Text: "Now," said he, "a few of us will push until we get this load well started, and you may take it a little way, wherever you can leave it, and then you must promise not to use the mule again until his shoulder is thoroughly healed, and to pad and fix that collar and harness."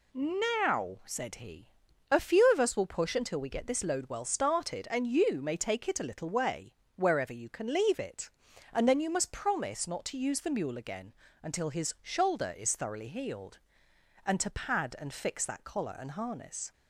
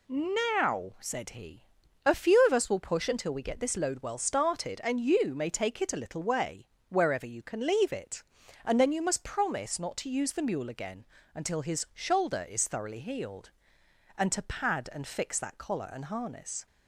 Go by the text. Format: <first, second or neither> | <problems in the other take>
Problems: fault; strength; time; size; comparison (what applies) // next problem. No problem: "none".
neither | pauses between "again" and "until"; slight; the same in both